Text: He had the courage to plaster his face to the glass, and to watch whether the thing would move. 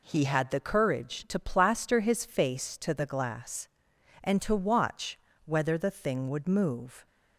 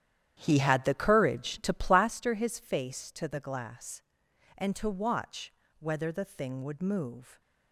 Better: first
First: pauses between "watch" and "whether"; slight; at 5.1 s; 0.28 s long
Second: starts louder than the rest; strong; until 2.1 s; 10.5 dB // pauses between "watch" and "whether"; slight; at 5.5 s; 0.28 s long

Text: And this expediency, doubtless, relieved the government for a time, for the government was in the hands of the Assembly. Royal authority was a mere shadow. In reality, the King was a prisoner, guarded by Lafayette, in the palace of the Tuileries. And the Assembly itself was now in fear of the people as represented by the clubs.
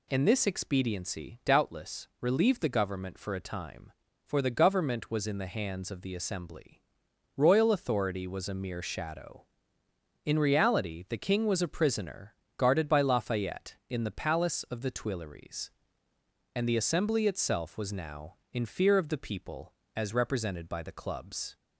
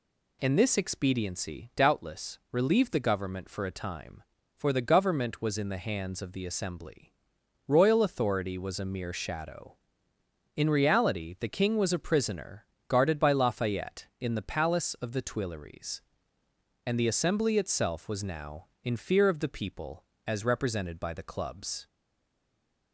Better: first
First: none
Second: stays silent after the last word; from 21.8 s on; 1.1 s long

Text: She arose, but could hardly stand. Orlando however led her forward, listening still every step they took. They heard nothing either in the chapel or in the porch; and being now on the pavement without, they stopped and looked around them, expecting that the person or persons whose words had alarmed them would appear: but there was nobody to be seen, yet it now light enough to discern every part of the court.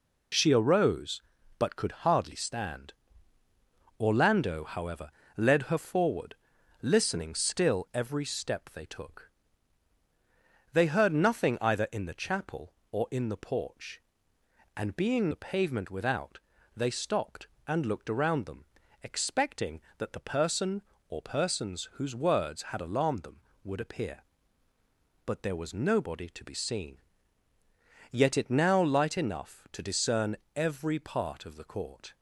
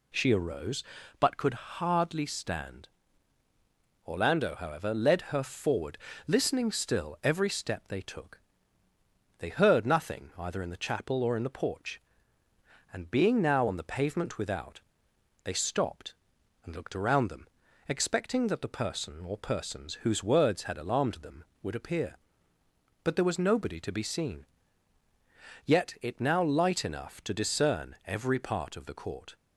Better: second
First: pauses between "however" and "led"; slight; at 5.1 s; 0.26 s long // skips "now on"; at 15.3 s // pauses between "discern" and "every"; slight; at 30.3 s; 0.22 s long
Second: none

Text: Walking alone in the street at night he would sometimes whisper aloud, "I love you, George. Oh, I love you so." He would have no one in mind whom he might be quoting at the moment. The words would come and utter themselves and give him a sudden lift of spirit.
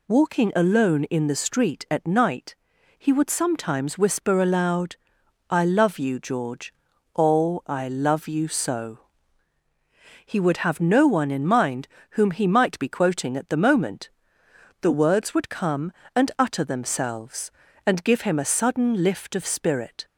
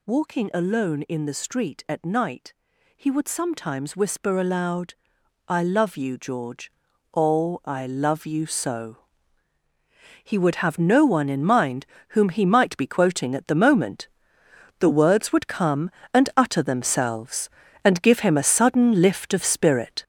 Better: first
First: pauses between "night" and "he"; at 2.5 s; 0.44 s long // pauses between "mind" and "whom"; slight; at 11.8 s; 0.32 s long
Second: gets louder; strong; throughout; 7.5 dB // pauses between "night" and "he"; at 2.5 s; 0.44 s long // pauses between "mind" and "whom"; slight; at 11.8 s; 0.32 s long

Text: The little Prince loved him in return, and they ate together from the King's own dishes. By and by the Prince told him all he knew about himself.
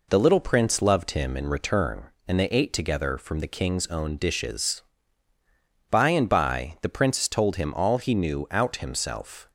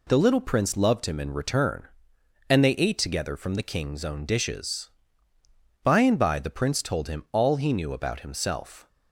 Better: second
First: says "out" for "about"; at 8.5 s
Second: none

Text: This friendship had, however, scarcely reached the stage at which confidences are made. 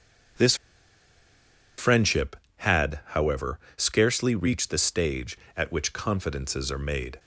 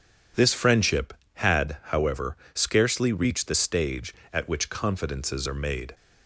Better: second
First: pauses between "This" and "friendship"; at 0.5 s; 1.2 s long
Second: none

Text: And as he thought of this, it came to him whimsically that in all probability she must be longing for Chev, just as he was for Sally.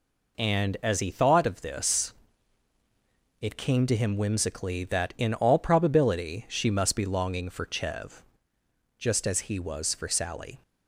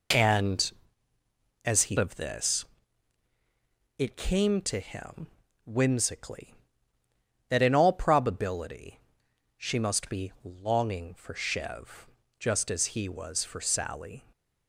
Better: first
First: none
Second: skips "thought"; at 1.9 s // pauses between "him" and "whimsically"; at 5.2 s; 0.38 s long // pauses between "probability" and "she"; noticeable; at 9.0 s; 0.56 s long

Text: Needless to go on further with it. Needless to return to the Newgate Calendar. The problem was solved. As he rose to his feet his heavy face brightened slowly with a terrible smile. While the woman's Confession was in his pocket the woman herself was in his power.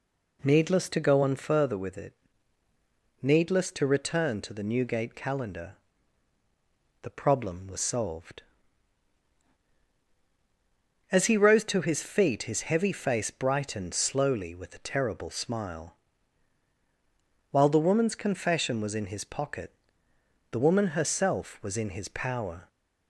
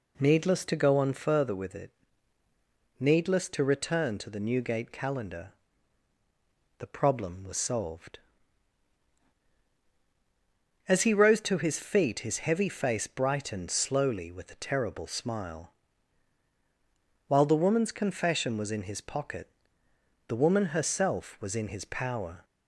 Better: neither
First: pauses between "pocket" and "the"; noticeable; at 19.7 s; 0.80 s long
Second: pauses between "pocket" and "the"; noticeable; at 19.4 s; 0.80 s long

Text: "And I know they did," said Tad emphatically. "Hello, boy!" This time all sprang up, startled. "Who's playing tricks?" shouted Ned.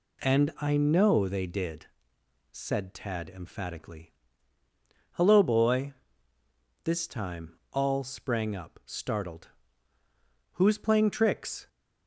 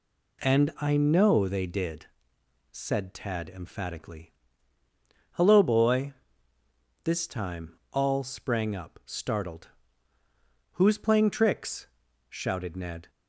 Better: second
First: stops before "shouted Ned"; at 11.6 s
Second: none

